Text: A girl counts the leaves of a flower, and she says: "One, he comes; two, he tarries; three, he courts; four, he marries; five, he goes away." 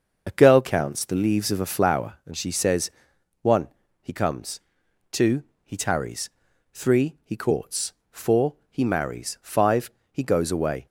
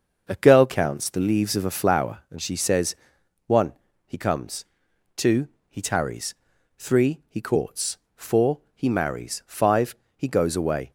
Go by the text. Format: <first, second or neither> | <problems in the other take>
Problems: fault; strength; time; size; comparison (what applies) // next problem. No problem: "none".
second | loses the start of "A"; at 0.2 s; 25 ms // starts louder than the rest; noticeable; until 1.2 s; 6 dB; noticeable in the second